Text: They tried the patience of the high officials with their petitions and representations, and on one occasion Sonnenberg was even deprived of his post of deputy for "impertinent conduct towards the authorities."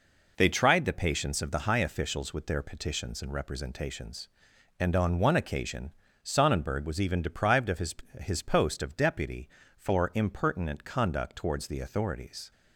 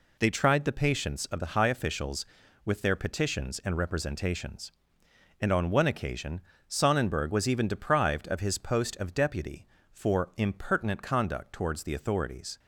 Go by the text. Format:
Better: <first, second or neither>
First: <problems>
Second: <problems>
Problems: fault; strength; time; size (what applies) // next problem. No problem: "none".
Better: second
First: pauses between "occasion" and "Sonnenberg"; slight; at 5.9 s; 0.30 s long // says "his" twice; at 8.1 s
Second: pauses between "occasion" and "Sonnenberg"; slight; at 6.3 s; 0.28 s long